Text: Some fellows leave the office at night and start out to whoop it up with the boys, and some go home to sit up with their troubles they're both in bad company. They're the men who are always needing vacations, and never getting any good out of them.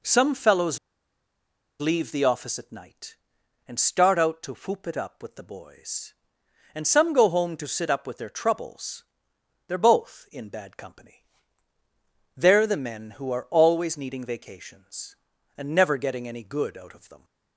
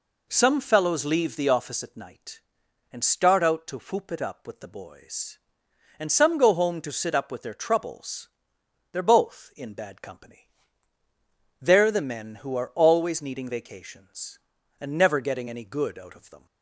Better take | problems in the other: second | pauses between "fellows" and "leave"; at 0.7 s; 1.0 s long // pauses between "troubles" and "they're"; noticeable; at 9.0 s; 0.62 s long; noticeable in the second

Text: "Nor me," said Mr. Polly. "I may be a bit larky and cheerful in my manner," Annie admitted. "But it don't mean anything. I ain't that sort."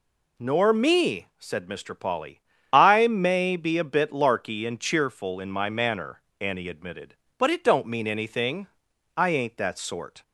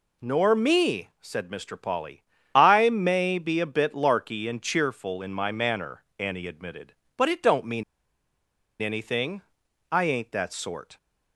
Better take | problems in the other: first | pauses between "mean" and "anything"; noticeable; at 7.8 s; 0.97 s long

